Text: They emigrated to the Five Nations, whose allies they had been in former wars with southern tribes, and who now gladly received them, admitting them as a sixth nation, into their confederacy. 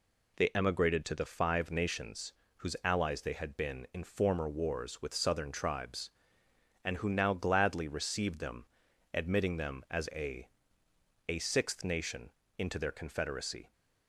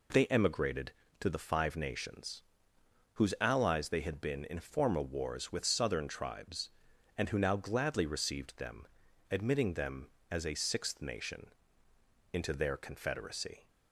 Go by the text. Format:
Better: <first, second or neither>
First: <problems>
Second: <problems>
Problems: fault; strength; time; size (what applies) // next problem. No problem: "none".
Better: second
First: says "a" twice; at 11.2 s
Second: none